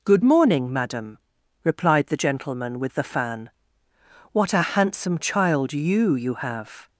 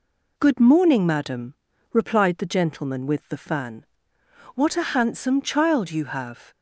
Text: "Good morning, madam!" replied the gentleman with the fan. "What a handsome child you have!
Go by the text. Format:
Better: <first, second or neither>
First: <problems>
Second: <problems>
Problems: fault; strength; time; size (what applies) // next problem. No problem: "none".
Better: second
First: says "you" twice; at 6.1 s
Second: none